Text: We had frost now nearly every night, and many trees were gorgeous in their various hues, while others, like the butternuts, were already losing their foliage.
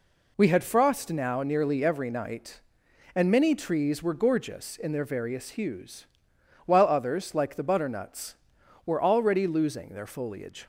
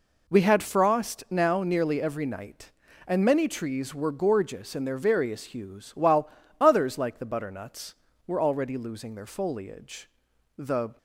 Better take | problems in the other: first | pauses between "while" and "others"; slight; at 6.2 s; 0.30 s long // goes on to say "The"; slight; from 10.5 s on; 0.40 s long

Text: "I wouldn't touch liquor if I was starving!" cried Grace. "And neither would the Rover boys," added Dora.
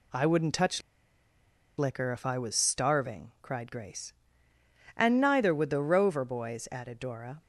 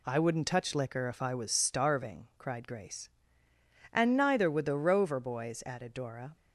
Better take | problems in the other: second | pauses between "touch" and "liquor"; noticeable; at 0.8 s; 0.97 s long

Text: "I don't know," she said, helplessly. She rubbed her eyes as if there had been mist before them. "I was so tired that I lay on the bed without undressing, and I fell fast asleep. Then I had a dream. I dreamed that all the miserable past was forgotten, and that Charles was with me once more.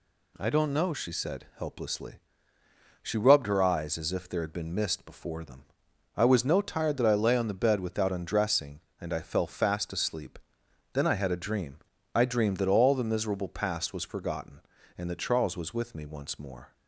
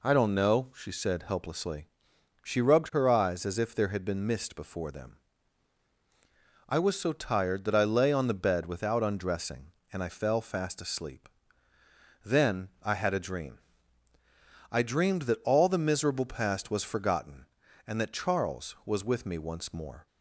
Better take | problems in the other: second | says "no" for "so"; at 6.4 s

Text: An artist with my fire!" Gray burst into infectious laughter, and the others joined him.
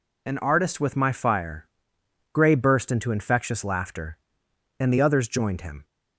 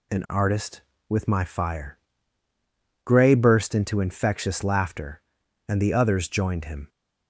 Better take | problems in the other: neither | none

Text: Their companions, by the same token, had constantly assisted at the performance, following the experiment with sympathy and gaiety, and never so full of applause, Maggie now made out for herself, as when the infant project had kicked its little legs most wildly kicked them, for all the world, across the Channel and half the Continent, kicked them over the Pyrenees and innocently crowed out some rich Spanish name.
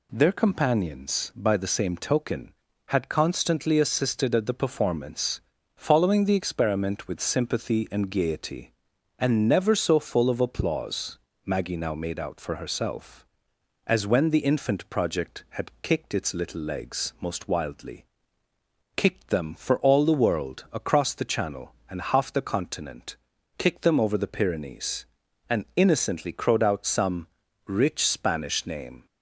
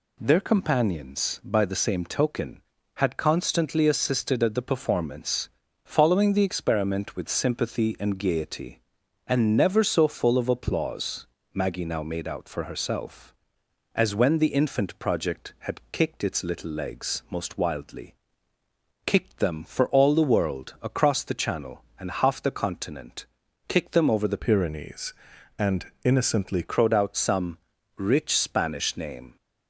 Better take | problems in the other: first | pauses between "wildly" and "kicked"; noticeable; at 18.1 s; 0.90 s long; noticeable in the first // changes voice from "Pyrenees" to "innocently"; from 24.3 to 26.6 s; 2.3 s long // pauses between "some" and "rich"; at 27.5 s; 0.38 s long; also in the first

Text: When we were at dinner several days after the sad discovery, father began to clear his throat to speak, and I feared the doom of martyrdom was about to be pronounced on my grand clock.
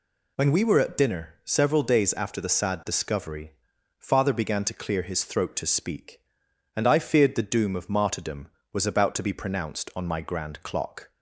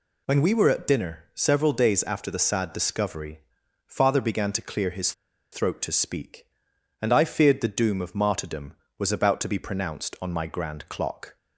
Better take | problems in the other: first | pauses between "his" and "throat"; at 5.1 s; 0.39 s long

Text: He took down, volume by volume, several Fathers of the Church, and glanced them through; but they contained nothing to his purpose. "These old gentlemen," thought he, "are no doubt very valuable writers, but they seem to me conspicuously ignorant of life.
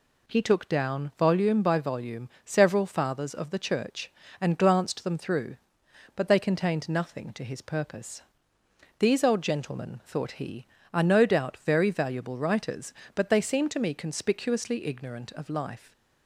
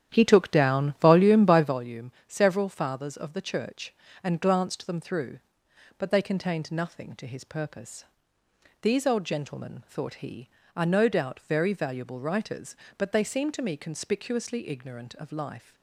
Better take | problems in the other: first | starts louder than the rest; strong; until 1.8 s; 10 dB

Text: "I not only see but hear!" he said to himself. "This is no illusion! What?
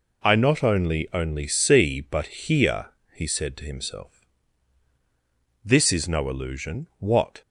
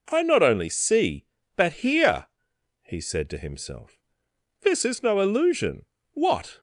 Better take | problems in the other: second | says "only" twice; at 1.1 s

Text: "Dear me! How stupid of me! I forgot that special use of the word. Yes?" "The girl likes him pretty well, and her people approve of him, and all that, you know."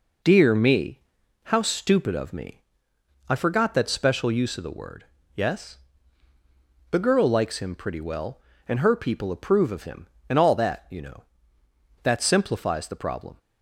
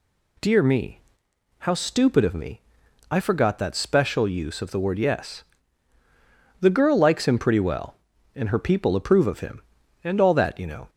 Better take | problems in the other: second | goes on to say "That simplifies the problem"; from 12.0 s on; 1.3 s long

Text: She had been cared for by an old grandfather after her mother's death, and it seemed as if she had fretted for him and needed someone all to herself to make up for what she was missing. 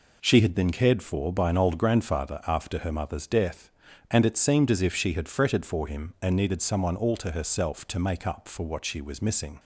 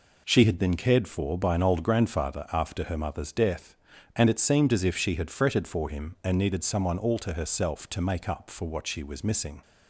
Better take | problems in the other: neither | none

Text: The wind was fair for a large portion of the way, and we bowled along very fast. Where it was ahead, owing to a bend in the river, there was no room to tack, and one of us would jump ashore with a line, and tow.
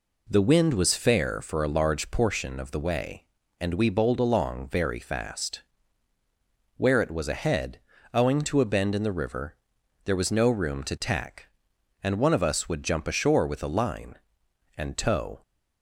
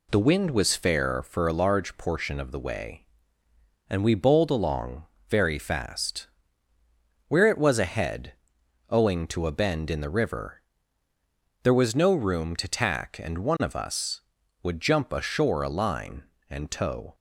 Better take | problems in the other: first | pauses between "along" and "very"; slight; at 5.0 s; 0.24 s long // skips "with"; at 15.6 s

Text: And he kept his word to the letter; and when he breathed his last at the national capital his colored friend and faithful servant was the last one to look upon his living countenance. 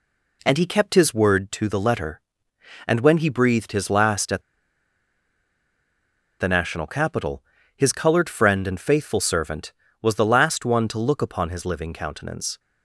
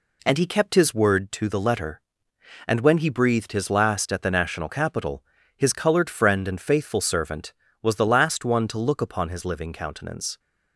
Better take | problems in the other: second | pauses between "at" and "the"; strong; at 4.4 s; 1.9 s long // pauses between "capital" and "his"; slight; at 7.4 s; 0.34 s long; slight in the second

